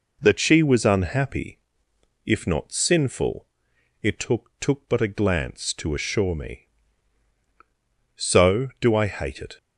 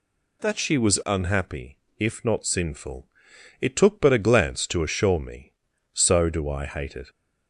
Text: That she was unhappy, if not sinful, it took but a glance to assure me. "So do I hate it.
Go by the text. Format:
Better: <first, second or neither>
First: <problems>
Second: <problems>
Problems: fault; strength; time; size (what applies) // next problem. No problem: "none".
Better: second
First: says "took" twice; at 4.5 s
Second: none